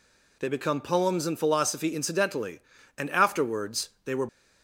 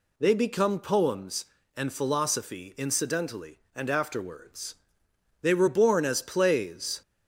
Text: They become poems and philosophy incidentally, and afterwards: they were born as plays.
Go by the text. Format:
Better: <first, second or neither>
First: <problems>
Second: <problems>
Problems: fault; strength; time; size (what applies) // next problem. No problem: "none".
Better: second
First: stops before "born as plays"; at 4.2 s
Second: none